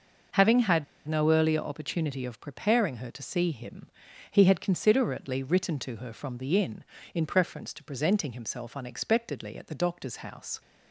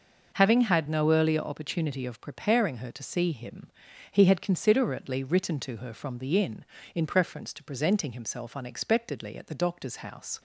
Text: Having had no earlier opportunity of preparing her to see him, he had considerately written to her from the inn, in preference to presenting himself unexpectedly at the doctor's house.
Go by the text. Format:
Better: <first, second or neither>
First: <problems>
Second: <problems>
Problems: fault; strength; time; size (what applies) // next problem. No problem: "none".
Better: second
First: pauses between "had" and "no"; slight; at 0.8 s; 0.23 s long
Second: none